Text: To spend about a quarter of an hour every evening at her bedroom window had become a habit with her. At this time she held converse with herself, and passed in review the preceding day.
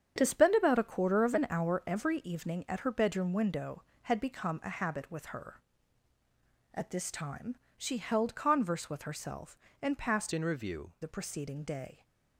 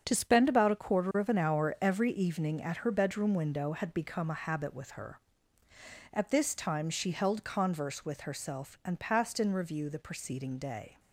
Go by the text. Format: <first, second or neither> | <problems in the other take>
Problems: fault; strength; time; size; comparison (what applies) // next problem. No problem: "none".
second | starts louder than the rest; strong; until 1.1 s; 8 dB; also in the second // pauses between "time" and "she"; slight; at 7.5 s; 0.22 s long // changes voice from "in" to "review"; from 10.3 to 10.9 s; 0.6 s long